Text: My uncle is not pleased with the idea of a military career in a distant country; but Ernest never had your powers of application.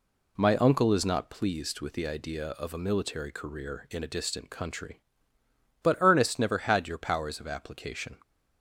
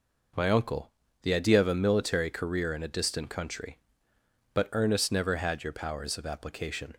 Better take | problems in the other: first | skips "is not pleased with"; at 1.0 s

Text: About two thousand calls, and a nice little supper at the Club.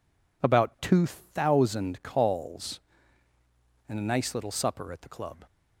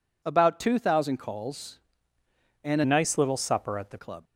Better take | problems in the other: first | changes voice from "nice" to "the"; from 2.8 to 3.9 s; 1.1 s long

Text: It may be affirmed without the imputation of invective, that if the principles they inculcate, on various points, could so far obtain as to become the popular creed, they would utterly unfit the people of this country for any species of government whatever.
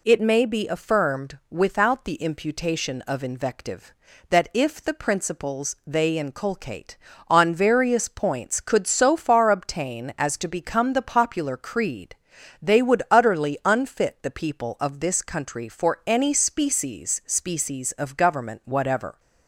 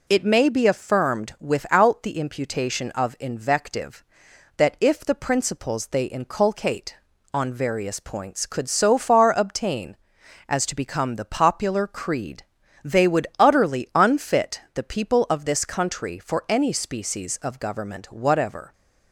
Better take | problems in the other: second | says "species" twice; at 17.2 s

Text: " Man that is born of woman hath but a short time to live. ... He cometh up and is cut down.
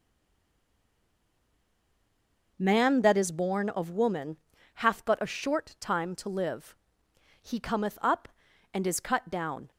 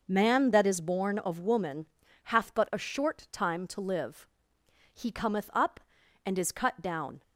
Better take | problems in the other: second | stays silent before the first word; strong; until 2.5 s; 2.5 s long // pauses between "woman" and "hath"; at 4.3 s; 0.38 s long; also in the second

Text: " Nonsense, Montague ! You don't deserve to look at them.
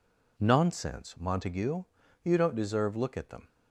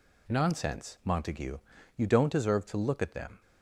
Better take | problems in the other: second | skips "to"; at 2.9 s

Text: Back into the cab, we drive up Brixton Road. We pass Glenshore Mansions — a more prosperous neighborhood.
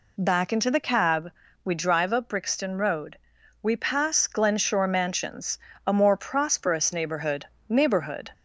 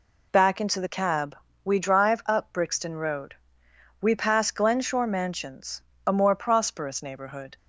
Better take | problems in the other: second | says "neighborhood" twice; at 7.6 s

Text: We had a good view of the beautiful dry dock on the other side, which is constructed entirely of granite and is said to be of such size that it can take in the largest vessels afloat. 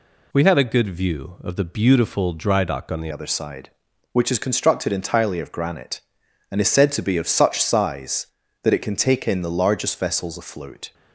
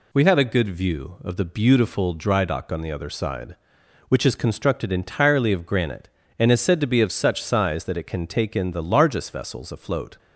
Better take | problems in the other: second | changes voice at "other"; from 3.1 s on; 7.8 s long

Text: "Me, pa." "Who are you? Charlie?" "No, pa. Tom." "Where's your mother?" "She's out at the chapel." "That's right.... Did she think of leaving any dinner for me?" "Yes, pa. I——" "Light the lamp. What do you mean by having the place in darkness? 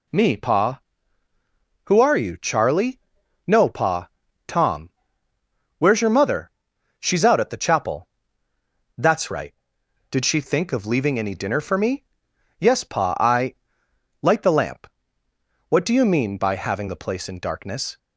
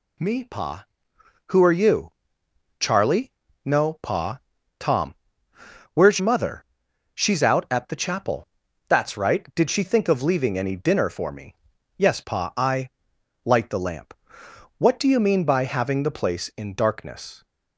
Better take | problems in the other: first | skips "your"; at 6.1 s

